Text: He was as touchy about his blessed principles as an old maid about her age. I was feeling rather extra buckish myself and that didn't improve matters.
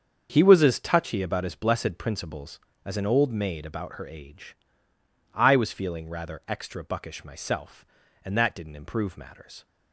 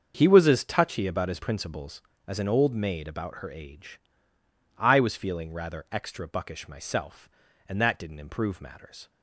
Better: first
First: starts louder than the rest; until 1.3 s; 7 dB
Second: starts louder than the rest; until 1.1 s; 6.5 dB // skips "blessed"; at 1.4 s

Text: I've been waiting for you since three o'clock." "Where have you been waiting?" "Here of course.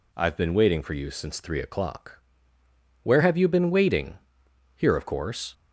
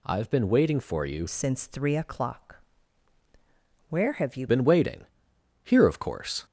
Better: first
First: none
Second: changes voice from "since" to "you"; from 1.2 to 4.4 s; 3.2 s long

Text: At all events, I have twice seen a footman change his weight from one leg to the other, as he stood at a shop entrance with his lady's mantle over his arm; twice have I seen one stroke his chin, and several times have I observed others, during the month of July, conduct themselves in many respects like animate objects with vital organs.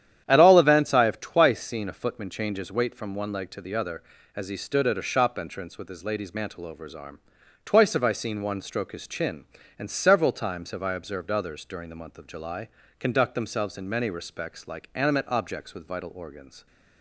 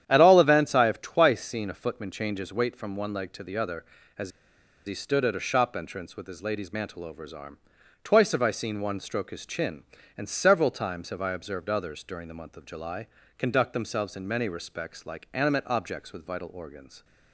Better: first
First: starts louder than the rest; strong; until 1.2 s; 10 dB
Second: starts louder than the rest; strong; until 1.0 s; 10 dB // pauses between "as" and "he"; noticeable; at 4.2 s; 0.57 s long

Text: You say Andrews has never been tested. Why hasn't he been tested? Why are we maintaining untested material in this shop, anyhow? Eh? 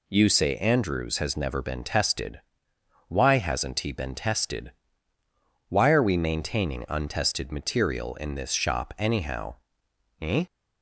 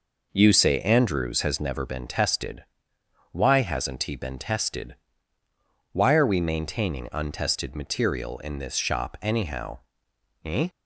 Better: first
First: none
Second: starts louder than the rest; noticeable; until 1.7 s; 5 dB

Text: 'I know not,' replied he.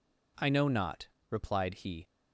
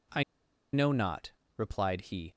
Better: first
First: none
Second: pauses between "I" and "know"; noticeable; at 0.2 s; 0.49 s long

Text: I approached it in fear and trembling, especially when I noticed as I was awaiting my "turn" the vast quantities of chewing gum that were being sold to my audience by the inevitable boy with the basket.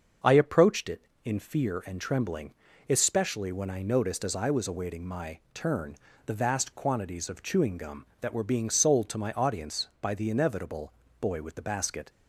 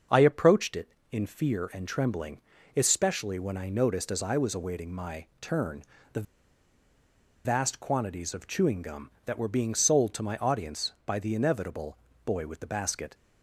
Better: first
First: starts louder than the rest; until 1.4 s; 6 dB // pauses between "my" and "turn"; slight; at 5.3 s; 0.16 s long // pauses between "turn" and "the"; slight; at 5.9 s; 0.32 s long // pauses between "inevitable" and "boy"; slight; at 10.9 s; 0.26 s long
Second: starts louder than the rest; until 1.3 s; 6 dB // pauses between "my" and "turn"; slight; at 5.2 s; 0.16 s long // pauses between "turn" and "the"; slight; at 5.8 s; 0.32 s long // pauses between "the" and "vast"; at 6.2 s; 1.2 s long // pauses between "inevitable" and "boy"; slight; at 11.9 s; 0.26 s long

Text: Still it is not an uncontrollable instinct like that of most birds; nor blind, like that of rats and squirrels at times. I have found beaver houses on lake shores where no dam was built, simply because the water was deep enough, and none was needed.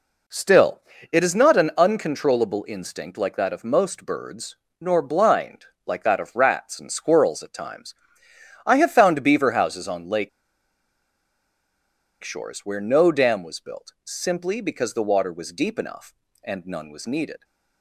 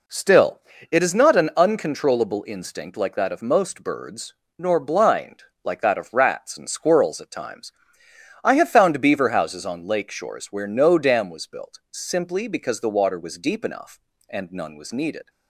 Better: second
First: pauses between "Still" and "it"; slight; at 0.8 s; 0.32 s long // pauses between "lake" and "shores"; strong; at 10.2 s; 1.9 s long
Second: pauses between "Still" and "it"; slight; at 0.5 s; 0.32 s long

